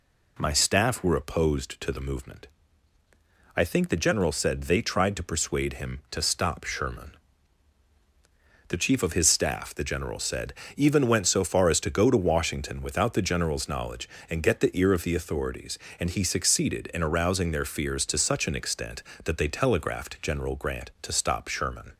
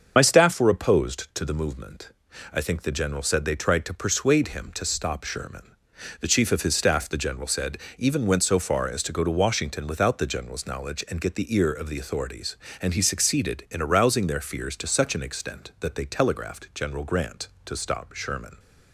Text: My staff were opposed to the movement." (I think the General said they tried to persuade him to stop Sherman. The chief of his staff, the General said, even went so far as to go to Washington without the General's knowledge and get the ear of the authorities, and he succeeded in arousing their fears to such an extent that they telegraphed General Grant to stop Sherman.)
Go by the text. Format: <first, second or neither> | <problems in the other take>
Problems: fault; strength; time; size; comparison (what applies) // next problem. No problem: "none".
first | loses the start of "My"; at 0.1 s; 55 ms // starts louder than the rest; until 1.1 s; 7 dB